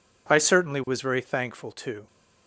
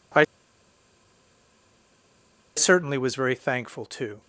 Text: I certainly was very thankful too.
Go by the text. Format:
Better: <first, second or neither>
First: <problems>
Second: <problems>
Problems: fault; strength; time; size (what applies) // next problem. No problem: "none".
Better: first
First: none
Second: pauses between "I" and "certainly"; strong; at 0.2 s; 2.3 s long